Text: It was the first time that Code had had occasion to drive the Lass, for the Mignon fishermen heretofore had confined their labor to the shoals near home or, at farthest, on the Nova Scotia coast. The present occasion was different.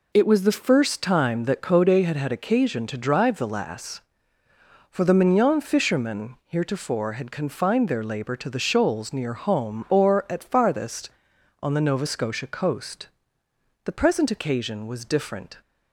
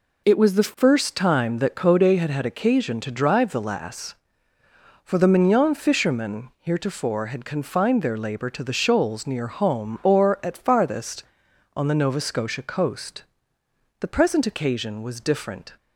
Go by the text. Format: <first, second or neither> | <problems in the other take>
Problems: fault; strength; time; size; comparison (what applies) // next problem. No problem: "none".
neither | none